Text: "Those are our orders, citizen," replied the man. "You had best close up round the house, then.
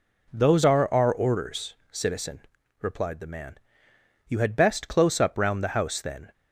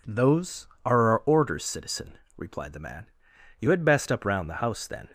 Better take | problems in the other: first | skips "close"; at 4.1 s

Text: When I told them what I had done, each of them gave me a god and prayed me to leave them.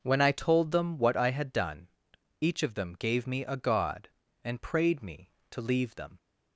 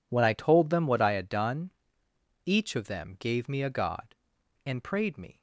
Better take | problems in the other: first | stops before "to leave them"; at 5.3 s

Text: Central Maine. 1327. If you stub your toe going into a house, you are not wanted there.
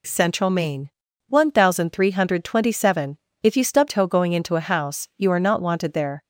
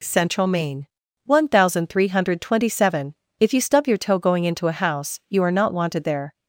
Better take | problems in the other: second | skips "your"; at 3.8 s

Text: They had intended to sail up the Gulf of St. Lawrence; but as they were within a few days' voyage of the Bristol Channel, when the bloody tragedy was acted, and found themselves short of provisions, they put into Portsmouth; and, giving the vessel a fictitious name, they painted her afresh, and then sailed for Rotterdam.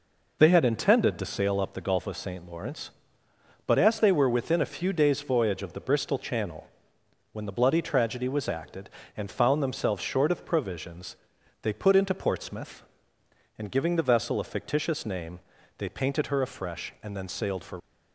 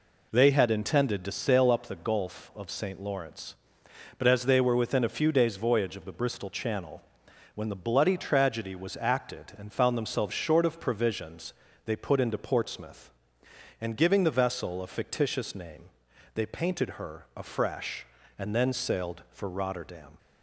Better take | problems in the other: second | stops before "Rotterdam"; at 17.7 s

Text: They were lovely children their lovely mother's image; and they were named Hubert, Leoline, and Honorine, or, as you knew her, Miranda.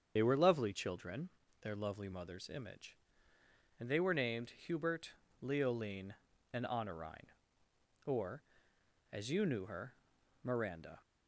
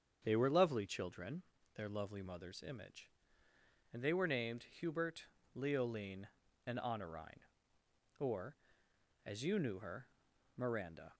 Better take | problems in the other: second | loses the start of "They"; at 0.1 s; 50 ms // starts louder than the rest; strong; until 1.1 s; 7.5 dB; strong in the second // pauses between "children" and "their"; slight; at 1.2 s; 0.34 s long; slight in the second

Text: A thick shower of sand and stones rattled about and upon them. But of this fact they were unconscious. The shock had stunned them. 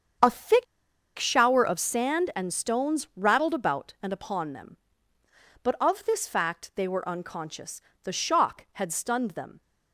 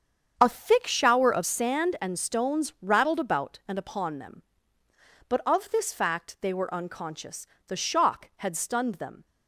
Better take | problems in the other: second | starts louder than the rest; strong; until 1.7 s; 7.5 dB; strong in the second // pauses between "thick" and "shower"; noticeable; at 0.6 s; 0.54 s long

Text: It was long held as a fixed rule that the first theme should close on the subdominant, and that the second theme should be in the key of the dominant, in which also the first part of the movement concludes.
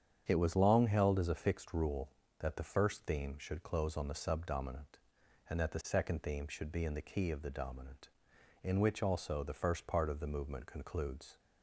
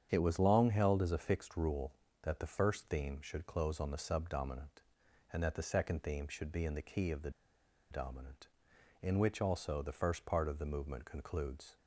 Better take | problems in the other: first | starts louder than the rest; strong; until 1.1 s; 8 dB; strong in the first // pauses between "the" and "dominant"; noticeable; at 7.3 s; 0.60 s long

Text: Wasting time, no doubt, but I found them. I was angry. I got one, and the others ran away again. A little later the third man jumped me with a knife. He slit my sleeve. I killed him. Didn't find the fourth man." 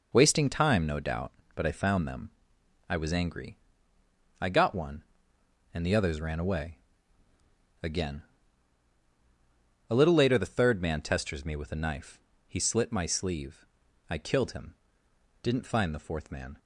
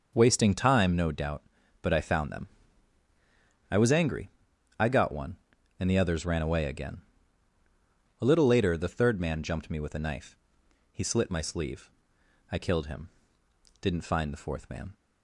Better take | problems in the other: second | pauses between "away" and "again"; at 6.7 s; 1.0 s long // says "testers" for "jumped"; at 10.9 s

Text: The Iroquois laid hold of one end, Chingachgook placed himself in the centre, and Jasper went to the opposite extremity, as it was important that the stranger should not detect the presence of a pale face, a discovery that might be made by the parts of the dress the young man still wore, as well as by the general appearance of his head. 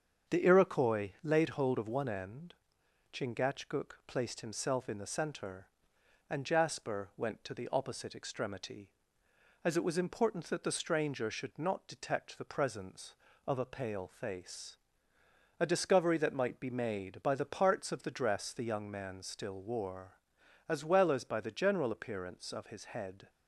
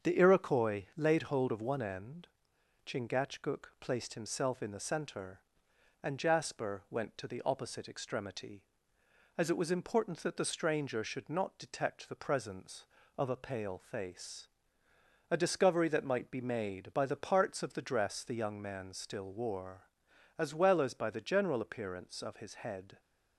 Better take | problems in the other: neither | starts louder than the rest; strong; the same in both

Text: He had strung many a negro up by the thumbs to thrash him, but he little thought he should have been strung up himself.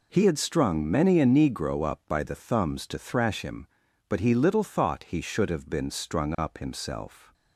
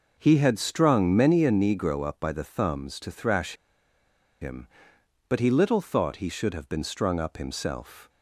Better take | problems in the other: first | pauses between "thrash" and "him"; noticeable; at 3.5 s; 0.88 s long

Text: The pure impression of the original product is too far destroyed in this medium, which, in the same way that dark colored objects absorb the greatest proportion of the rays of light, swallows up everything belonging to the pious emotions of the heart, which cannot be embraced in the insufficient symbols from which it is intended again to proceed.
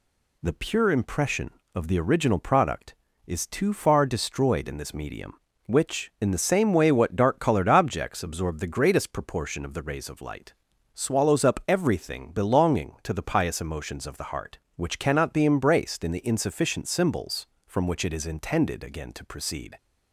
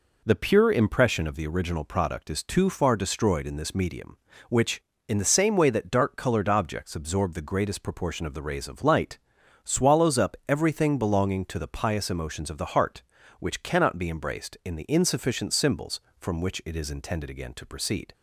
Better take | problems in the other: second | says "what" for "that"; at 6.9 s

